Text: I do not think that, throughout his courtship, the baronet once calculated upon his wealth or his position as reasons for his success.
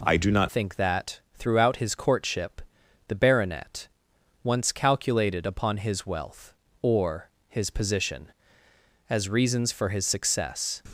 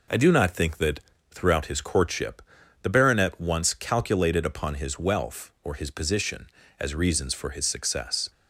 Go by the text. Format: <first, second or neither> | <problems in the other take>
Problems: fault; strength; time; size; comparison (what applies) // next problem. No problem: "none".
second | changes voice at "think"; from 0.4 s on; 10.4 s long // pauses between "baronet" and "once"; noticeable; at 3.8 s; 0.56 s long // pauses between "or" and "his"; slight; at 7.2 s; 0.18 s long